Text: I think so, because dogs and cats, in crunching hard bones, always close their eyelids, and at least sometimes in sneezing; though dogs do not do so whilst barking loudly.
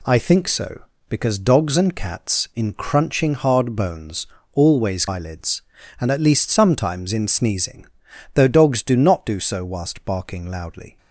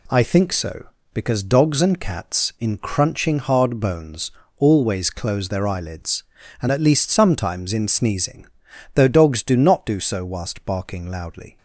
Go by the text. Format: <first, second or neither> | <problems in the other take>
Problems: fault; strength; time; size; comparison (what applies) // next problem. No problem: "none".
second | skips "close their"; at 5.0 s